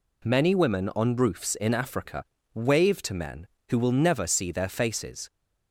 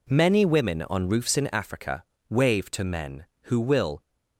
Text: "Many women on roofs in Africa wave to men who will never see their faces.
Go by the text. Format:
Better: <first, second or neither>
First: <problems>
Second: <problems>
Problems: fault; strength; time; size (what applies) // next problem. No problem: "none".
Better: first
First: pauses between "Africa" and "wave"; slight; at 2.2 s; 0.32 s long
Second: pauses between "Africa" and "wave"; slight; at 2.0 s; 0.28 s long // stops before "never see their faces"; at 4.0 s